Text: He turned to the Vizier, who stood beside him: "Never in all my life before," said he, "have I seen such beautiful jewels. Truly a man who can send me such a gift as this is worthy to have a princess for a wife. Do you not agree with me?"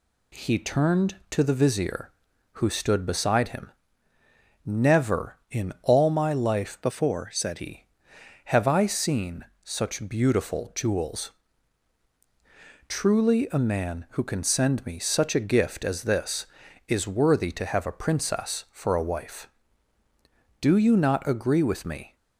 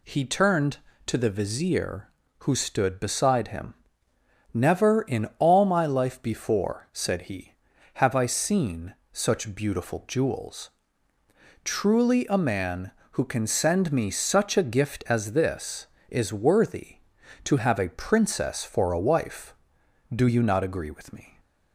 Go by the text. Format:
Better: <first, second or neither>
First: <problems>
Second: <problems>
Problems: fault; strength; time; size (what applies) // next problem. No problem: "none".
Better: second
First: changes voice from "before" to "said"; from 6.8 to 7.5 s; 0.7 s long // pauses between "seen" and "such"; slight; at 9.4 s; 0.18 s long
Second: pauses between "seen" and "such"; slight; at 8.9 s; 0.20 s long